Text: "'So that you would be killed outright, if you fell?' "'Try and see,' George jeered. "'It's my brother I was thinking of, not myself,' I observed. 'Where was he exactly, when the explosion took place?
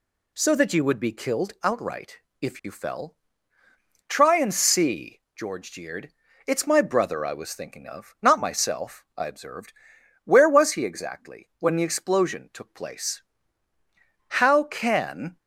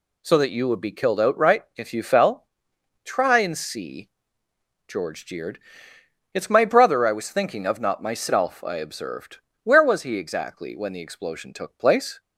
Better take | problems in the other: second | goes on to say "How can"; noticeable; from 14.2 s on; 1.1 s long

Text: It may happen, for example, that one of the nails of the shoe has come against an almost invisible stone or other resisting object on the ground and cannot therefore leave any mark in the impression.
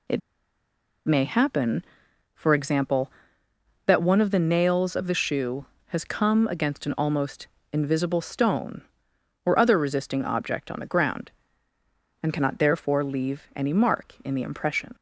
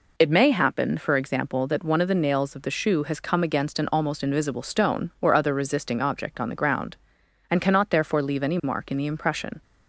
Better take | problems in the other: second | pauses between "It" and "may"; noticeable; at 0.2 s; 0.86 s long // pauses between "almost" and "invisible"; slight; at 7.4 s; 0.26 s long

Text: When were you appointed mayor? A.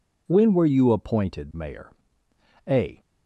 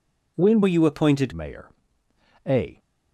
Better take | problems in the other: first | changes voice from "were" to "appointed"; from 0.6 to 1.3 s; 0.7 s long

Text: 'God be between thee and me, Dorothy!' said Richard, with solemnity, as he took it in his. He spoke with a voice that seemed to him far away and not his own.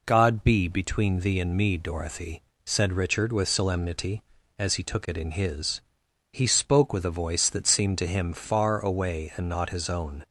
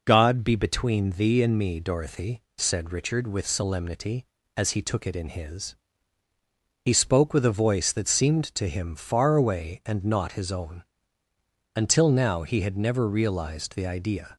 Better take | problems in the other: first | goes on to say "Until now he had never realized the idea"; strong; from 11.7 s on; 2.6 s long

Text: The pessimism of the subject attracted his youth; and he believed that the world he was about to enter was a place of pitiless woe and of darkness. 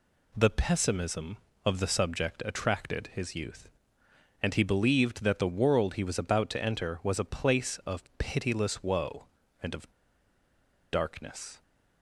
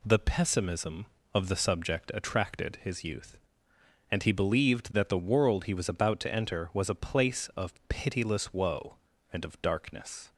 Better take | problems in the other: second | pauses between "of" and "darkness"; at 9.9 s; 1.0 s long

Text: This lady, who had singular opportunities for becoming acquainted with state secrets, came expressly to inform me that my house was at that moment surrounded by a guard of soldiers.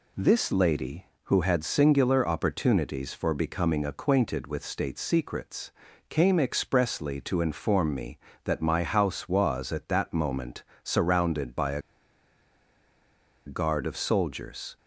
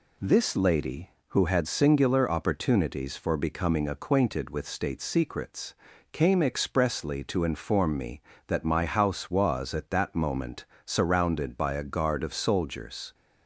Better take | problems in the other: second | pauses between "moment" and "surrounded"; slight; at 10.6 s; 0.20 s long; slight in the second // pauses between "a" and "guard"; strong; at 11.7 s; 1.6 s long

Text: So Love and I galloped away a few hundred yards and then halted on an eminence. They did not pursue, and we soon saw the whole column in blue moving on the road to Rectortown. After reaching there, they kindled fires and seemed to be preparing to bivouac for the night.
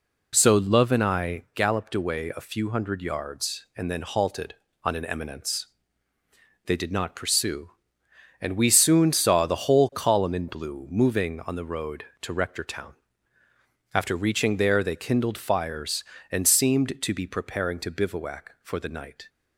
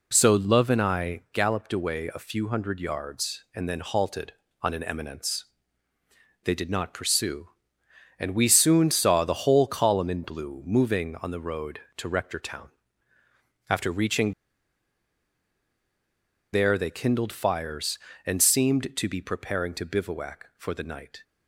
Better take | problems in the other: first | pauses between "reaching" and "there"; strong; at 14.3 s; 2.1 s long

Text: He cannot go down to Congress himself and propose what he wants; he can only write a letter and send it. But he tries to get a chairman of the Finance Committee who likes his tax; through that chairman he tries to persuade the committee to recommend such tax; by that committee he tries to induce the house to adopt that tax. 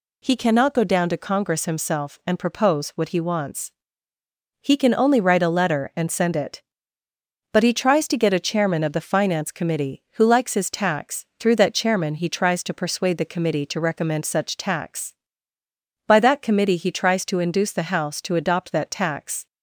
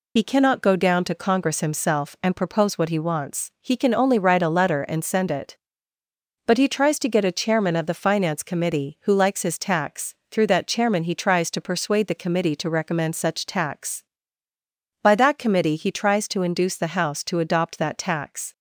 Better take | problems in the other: first | loses the start of "He"; at 0.1 s; 40 ms

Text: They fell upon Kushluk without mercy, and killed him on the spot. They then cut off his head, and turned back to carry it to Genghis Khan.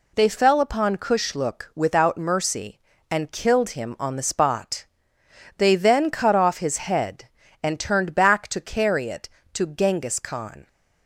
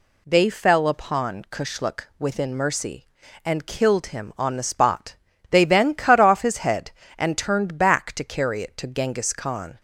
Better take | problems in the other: first | says "within" for "without"; at 2.1 s

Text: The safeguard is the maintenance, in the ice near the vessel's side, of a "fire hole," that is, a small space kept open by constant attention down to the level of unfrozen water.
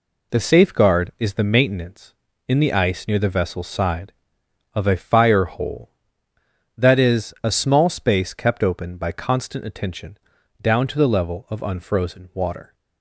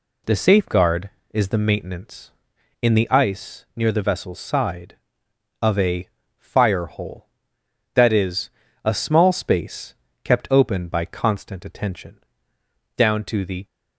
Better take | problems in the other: first | pauses between "a" and "fire"; slight; at 6.0 s; 0.30 s long // pauses between "space" and "kept"; slight; at 9.9 s; 0.30 s long // pauses between "attention" and "down"; noticeable; at 12.1 s; 0.76 s long; also in the first // stops before "level of unfrozen water"; at 13.6 s

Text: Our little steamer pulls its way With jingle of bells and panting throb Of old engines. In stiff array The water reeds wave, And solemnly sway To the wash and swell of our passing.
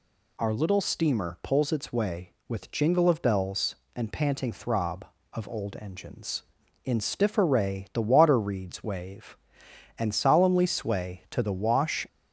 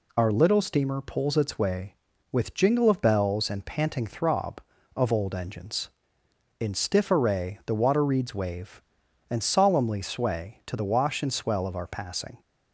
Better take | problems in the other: second | stops before "and swell of our passing"; at 12.0 s

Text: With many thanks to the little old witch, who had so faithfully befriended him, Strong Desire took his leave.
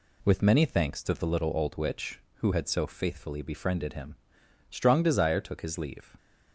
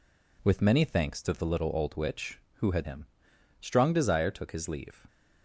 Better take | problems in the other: first | skips "so faithfully befriended"; at 2.8 s

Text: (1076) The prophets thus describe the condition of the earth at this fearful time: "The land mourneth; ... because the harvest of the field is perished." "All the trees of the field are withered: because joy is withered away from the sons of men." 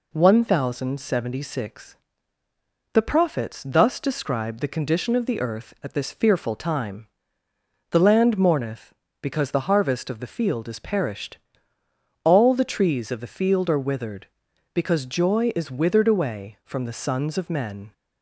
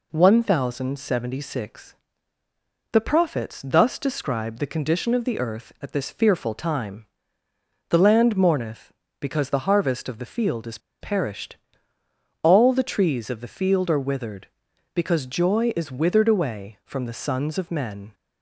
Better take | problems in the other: first | pauses between "is" and "perished"; slight; at 10.7 s; 0.22 s long

